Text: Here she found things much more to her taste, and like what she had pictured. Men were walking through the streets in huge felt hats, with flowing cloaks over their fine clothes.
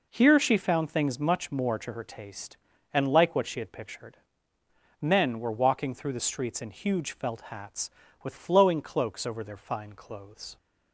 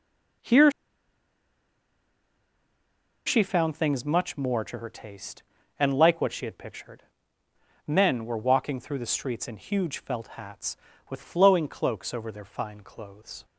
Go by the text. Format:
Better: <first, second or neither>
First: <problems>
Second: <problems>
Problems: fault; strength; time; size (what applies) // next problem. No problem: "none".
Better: first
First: none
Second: pauses between "Here" and "she"; strong; at 0.7 s; 2.5 s long